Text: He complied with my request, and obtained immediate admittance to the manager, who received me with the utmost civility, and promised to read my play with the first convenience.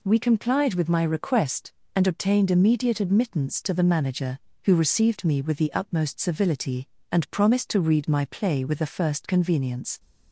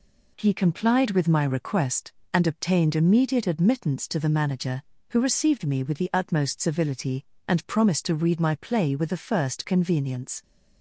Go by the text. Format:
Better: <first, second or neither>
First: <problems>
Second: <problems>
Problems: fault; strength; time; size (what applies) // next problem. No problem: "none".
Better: second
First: says "We" for "He"; at 0.0 s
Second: none